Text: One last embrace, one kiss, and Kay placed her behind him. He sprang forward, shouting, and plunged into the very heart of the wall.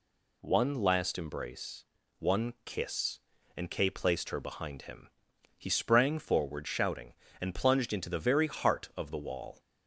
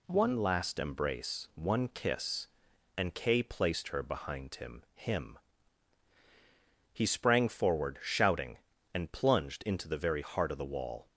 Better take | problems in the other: first | says "him" twice; at 4.9 s

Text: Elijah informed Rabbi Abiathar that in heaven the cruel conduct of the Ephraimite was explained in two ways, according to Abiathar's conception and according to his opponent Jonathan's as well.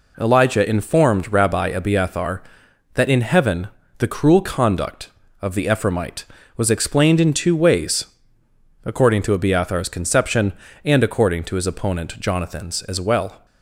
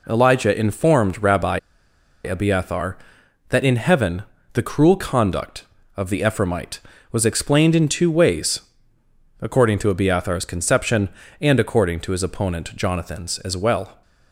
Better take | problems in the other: first | pauses between "Rabbi" and "Abiathar"; noticeable; at 1.5 s; 0.65 s long // pauses between "heaven" and "the"; slight; at 4.2 s; 0.30 s long; slight in the first

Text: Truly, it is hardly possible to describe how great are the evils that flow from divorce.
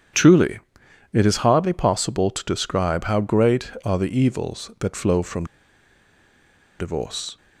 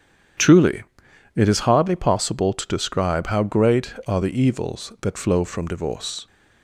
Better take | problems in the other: second | starts louder than the rest; strong; until 1.6 s; 9 dB; strong in the second // pauses between "from" and "divorce"; strong; at 5.4 s; 1.3 s long

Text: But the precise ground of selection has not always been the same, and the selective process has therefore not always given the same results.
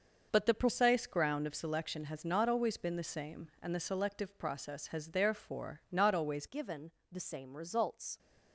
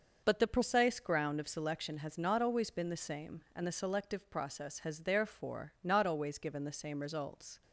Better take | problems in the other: second | starts louder than the rest; noticeable; until 1.3 s; 6 dB; also in the second // changes voice at "given"; from 6.4 s on; 1.7 s long // pauses between "given" and "the"; slight; at 6.9 s; 0.18 s long

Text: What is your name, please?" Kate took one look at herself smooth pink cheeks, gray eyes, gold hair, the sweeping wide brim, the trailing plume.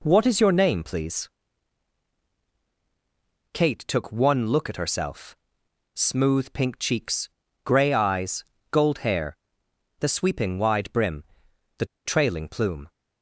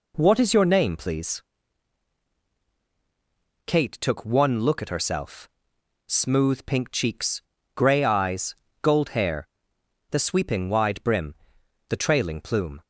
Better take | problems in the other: second | pauses between "herself" and "smooth"; noticeable; at 5.3 s; 0.58 s long; noticeable in the second // pauses between "the" and "trailing"; slight; at 11.8 s; 0.21 s long

